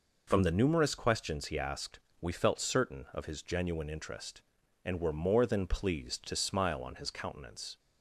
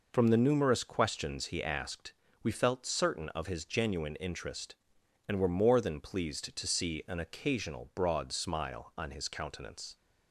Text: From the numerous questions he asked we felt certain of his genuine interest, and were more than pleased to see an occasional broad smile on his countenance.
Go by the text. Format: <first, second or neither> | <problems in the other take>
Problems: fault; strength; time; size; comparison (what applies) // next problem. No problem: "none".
second | pauses between "asked" and "we"; slight; at 2.0 s; 0.20 s long; slight in the second // skips "see an occasional broad"; at 6.3 s